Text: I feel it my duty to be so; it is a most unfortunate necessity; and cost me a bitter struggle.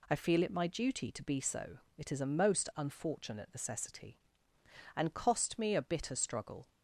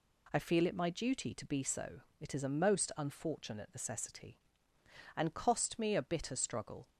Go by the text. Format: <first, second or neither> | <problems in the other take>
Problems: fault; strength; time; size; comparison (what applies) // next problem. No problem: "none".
neither | none